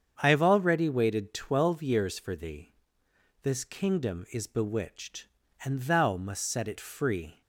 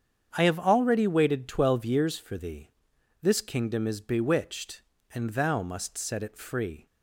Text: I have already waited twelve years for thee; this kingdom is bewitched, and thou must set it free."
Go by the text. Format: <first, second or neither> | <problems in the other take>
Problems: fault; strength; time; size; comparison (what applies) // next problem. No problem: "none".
neither | starts louder than the rest; strong; the same in both